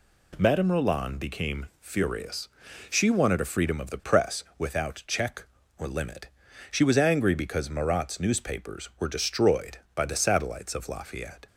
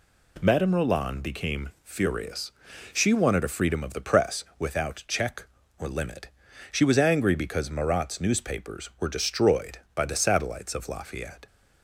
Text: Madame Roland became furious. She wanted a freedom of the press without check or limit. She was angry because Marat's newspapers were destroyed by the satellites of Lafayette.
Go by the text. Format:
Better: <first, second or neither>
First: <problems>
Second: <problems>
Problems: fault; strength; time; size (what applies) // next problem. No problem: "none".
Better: neither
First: none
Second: none